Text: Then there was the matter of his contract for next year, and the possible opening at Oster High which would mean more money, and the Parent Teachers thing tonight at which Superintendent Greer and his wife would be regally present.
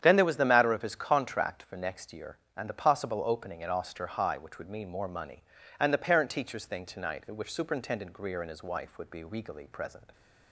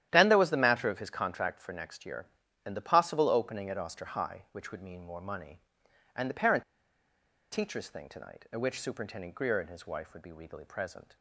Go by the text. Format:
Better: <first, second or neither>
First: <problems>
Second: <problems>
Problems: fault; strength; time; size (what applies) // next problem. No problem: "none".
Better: first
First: starts louder than the rest; strong; until 1.0 s; 9 dB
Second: starts louder than the rest; strong; until 1.1 s; 11.5 dB // pauses between "Parent" and "Teachers"; noticeable; at 6.6 s; 0.88 s long